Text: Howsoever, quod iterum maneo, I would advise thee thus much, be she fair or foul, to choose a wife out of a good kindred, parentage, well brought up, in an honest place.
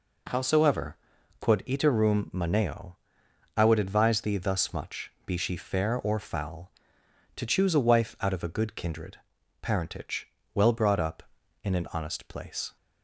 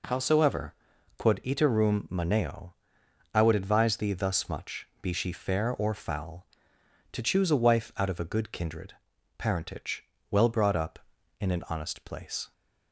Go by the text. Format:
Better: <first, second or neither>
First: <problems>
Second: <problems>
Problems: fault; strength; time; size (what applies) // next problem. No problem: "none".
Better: neither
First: none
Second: none